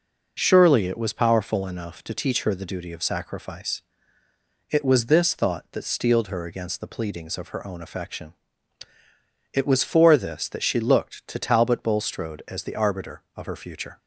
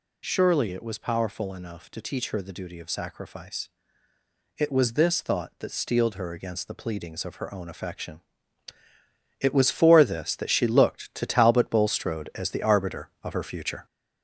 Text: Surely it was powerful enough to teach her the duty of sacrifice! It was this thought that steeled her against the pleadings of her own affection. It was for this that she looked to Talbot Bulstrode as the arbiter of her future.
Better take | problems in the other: first | gets louder; throughout; 4 dB

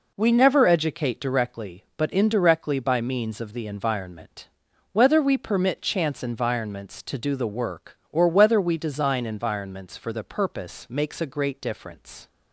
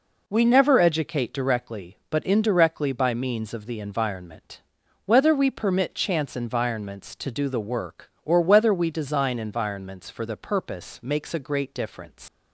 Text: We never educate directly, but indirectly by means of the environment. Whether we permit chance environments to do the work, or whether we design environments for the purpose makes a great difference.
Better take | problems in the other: first | leaves "difference" unfinished; at 12.2 s; 120 ms

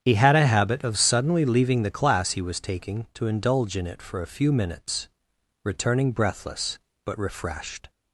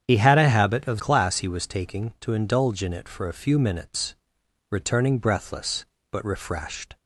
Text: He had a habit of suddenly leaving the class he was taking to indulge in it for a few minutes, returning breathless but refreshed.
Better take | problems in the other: first | starts louder than the rest; strong; until 1.0 s; 8.5 dB; strong in the first // skips "suddenly leaving the"; at 0.9 s

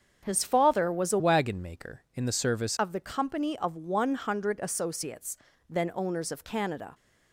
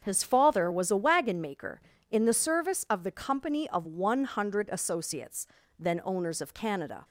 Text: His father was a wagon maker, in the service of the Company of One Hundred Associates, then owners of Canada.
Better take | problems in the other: second | starts louder than the rest; strong; until 1.2 s; 7 dB; strong in the second // changes voice from "wagon" to "service"; from 1.1 to 2.7 s; 1.6 s long

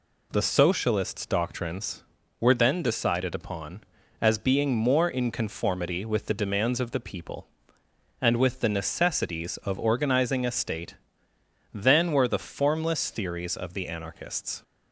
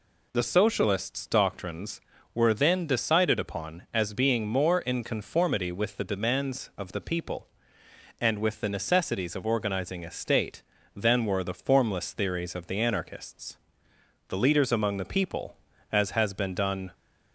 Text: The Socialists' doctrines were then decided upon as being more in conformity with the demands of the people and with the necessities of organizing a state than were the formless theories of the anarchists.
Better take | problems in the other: first | goes on to say "The leaders among the people as has been done"; strong; from 14.2 s on; 2.6 s long

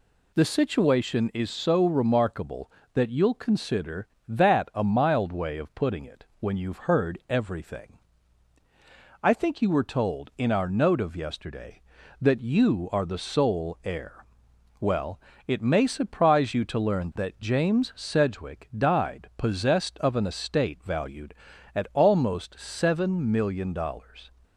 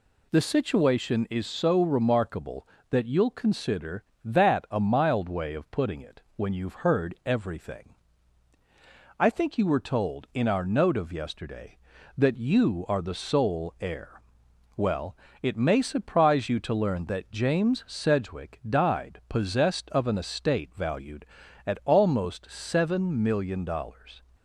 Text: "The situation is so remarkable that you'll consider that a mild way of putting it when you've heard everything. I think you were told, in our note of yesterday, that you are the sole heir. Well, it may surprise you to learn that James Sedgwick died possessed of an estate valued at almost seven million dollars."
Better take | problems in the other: neither | none

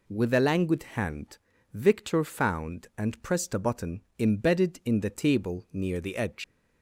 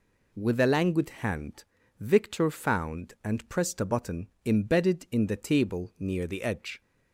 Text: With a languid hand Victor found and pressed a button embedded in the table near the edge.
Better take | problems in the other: second | pauses between "hand" and "Victor"; slight; at 1.3 s; 0.36 s long; slight in the second // pauses between "button" and "embedded"; slight; at 4.0 s; 0.18 s long; slight in the second // leaves "edge" unfinished; at 6.4 s; 95 ms

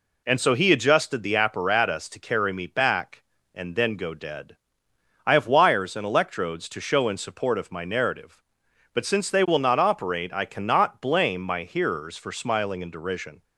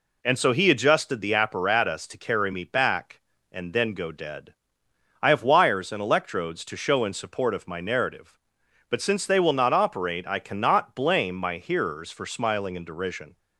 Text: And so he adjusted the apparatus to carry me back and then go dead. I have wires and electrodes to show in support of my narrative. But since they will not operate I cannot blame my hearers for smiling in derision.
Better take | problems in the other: neither | none

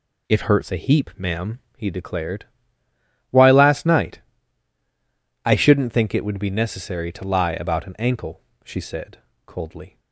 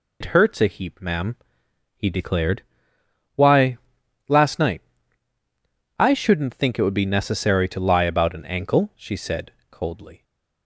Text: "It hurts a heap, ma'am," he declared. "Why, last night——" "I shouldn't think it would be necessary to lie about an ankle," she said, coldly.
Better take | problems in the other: first | loses the start of "It"; at 0.2 s; 90 ms

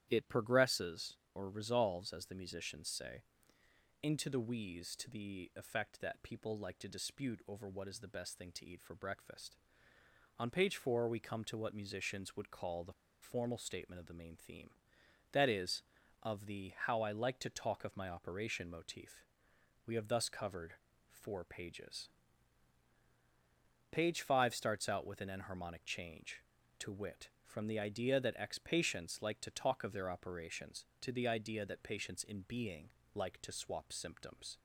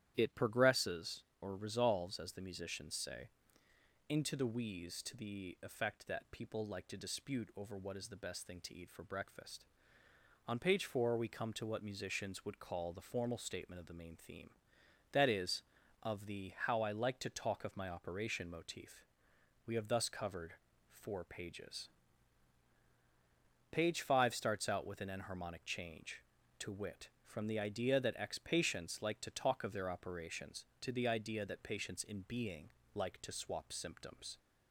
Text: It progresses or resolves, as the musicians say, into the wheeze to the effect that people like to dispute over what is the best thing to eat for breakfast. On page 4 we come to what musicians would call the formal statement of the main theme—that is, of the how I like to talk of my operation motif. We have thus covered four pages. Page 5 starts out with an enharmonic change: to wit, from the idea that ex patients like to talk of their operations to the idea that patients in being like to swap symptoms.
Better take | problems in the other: second | starts louder than the rest; strong; until 1.0 s; 11 dB; strong in the second // pauses between "the" and "formal"; slight; at 12.9 s; 0.28 s long // pauses between "covered" and "four"; slight; at 20.7 s; 0.36 s long; slight in the second // pauses between "being" and "like"; slight; at 32.9 s; 0.22 s long; slight in the second

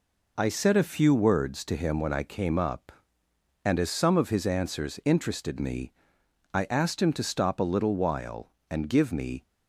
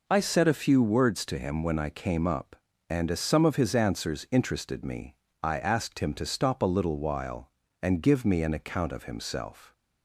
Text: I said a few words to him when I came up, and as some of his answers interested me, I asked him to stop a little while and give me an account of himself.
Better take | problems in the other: second | stops before "an account of himself"; at 9.4 s

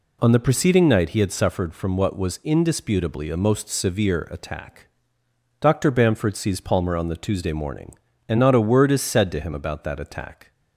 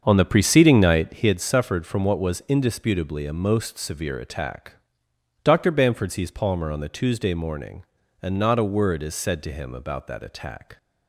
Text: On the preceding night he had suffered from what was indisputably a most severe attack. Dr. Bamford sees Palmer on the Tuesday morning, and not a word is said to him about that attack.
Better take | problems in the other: first | starts louder than the rest; until 1.2 s; 7 dB

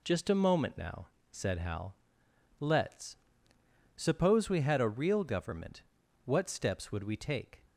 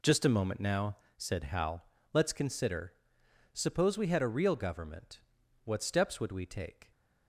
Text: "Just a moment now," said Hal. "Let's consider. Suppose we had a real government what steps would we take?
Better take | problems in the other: second | skips "consider"; at 3.5 s // pauses between "government" and "what"; at 5.8 s; 0.42 s long; also in the second

